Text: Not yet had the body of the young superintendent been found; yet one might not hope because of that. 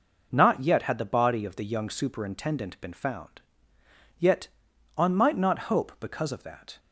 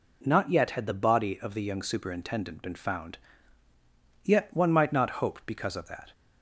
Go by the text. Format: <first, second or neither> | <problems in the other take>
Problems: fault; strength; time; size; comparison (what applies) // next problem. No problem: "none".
second | says "on" for "one"; at 4.9 s